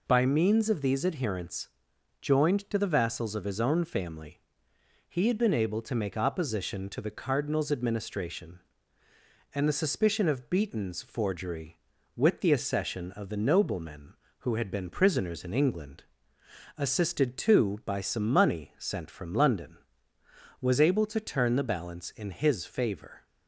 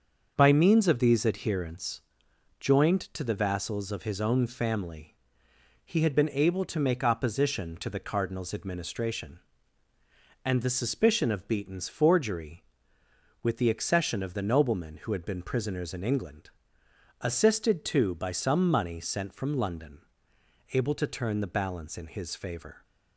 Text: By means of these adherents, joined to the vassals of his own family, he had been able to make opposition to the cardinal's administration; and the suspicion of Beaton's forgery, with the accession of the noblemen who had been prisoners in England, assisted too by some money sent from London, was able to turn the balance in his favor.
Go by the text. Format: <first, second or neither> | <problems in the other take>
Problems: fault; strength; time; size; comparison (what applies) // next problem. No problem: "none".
first | starts louder than the rest; until 1.3 s; 6.5 dB // skips "was"; at 20.3 s